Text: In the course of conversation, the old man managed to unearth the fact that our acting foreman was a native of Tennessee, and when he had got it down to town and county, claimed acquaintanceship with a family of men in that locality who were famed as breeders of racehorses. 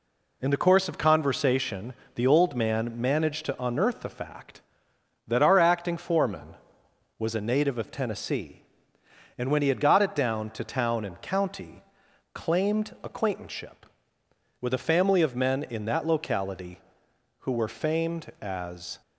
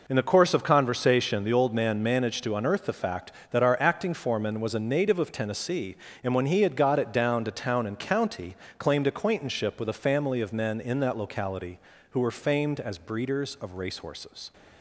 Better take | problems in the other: second | stops before "breeders of racehorses"; at 19.0 s

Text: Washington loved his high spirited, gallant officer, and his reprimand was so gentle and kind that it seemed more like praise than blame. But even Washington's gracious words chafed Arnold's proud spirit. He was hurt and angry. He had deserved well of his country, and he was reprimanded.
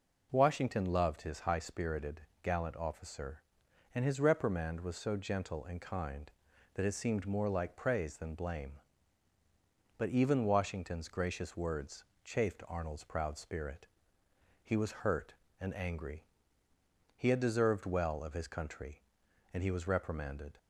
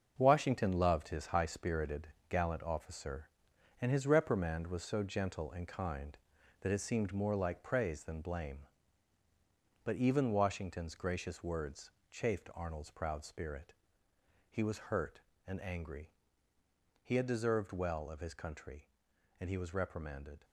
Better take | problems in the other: first | gets quieter; strong; throughout; 8.5 dB // pauses between "words" and "chafed"; slight; at 11.9 s; 0.20 s long; slight in the first

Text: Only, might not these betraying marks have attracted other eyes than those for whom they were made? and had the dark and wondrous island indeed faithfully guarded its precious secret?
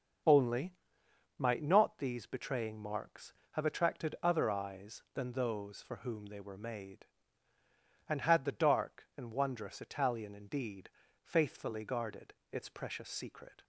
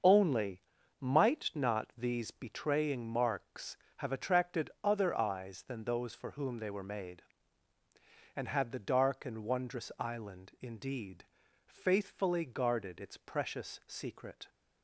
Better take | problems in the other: second | starts louder than the rest; until 1.8 s; 6.5 dB; also in the second // says "italian" for "island"; at 9.8 s // pauses between "indeed" and "faithfully"; slight; at 10.8 s; 0.34 s long; also in the second // pauses between "guarded" and "its"; slight; at 12.3 s; 0.18 s long

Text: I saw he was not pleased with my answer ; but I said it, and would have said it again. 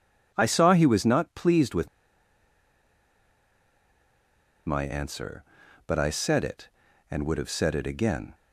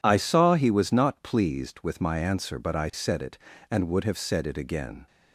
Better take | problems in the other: second | pauses between "with" and "my"; strong; at 1.8 s; 2.8 s long

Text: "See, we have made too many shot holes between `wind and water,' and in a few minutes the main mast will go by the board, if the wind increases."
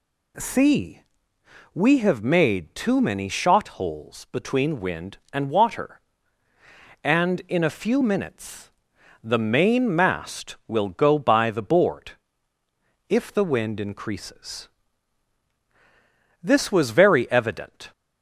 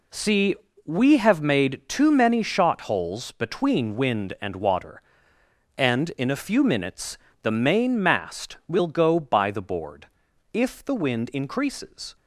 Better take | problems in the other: second | pauses between "minutes" and "the"; noticeable; at 8.6 s; 0.54 s long; slight in the second // goes on to say "This was very evident"; from 16.4 s on; 1.5 s long

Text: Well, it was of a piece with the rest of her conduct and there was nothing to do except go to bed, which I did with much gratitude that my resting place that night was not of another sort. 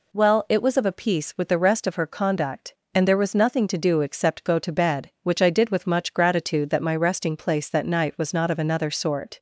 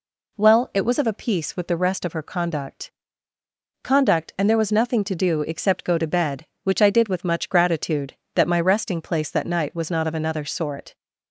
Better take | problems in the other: first | says "conduct" twice; at 3.8 s

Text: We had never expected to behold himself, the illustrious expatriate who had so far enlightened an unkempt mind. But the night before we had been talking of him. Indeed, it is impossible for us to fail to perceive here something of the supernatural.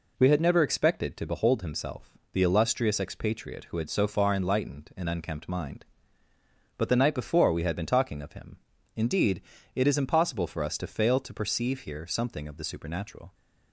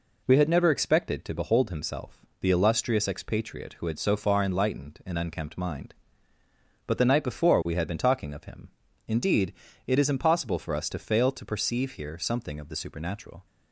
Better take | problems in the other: neither | none

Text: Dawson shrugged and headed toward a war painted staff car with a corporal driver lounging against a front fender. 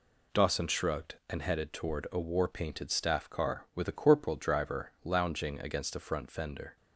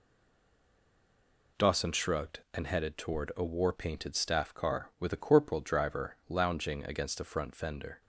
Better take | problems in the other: first | stays silent before the first word; noticeable; until 1.5 s; 1.5 s long

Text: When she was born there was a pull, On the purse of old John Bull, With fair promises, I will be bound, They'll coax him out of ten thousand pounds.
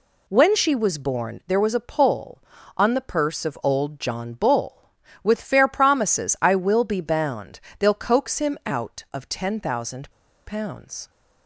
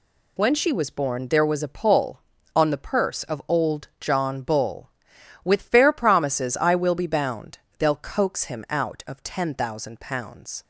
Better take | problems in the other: second | pauses between "thousand" and "pounds"; slight; at 10.1 s; 0.35 s long

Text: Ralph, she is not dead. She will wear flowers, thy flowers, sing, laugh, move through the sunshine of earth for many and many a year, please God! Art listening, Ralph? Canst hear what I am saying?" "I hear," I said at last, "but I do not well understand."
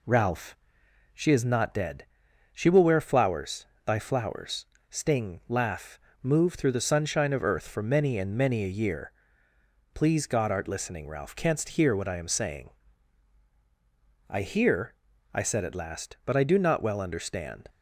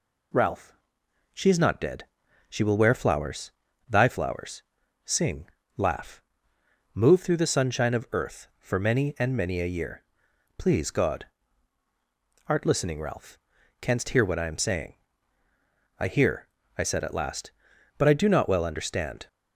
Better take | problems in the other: second | says "sting" for "sing"; at 4.8 s

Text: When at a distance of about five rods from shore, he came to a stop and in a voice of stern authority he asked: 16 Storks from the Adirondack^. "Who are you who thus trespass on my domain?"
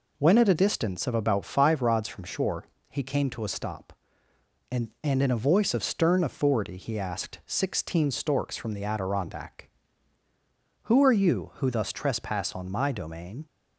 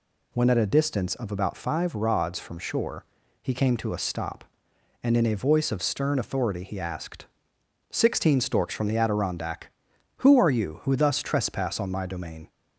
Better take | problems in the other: second | says "and" twice; at 5.0 s

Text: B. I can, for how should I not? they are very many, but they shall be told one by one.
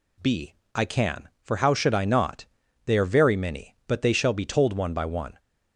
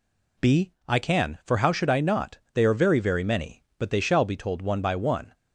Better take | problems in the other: first | says "very" twice; at 2.9 s

